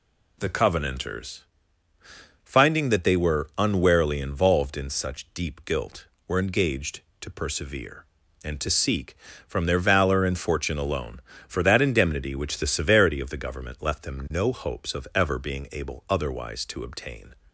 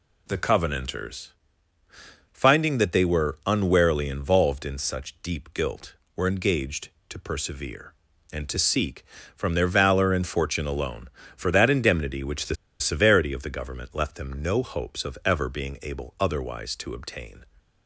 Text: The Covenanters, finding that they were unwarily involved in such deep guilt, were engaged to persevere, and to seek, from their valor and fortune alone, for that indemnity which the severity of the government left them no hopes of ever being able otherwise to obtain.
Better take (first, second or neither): first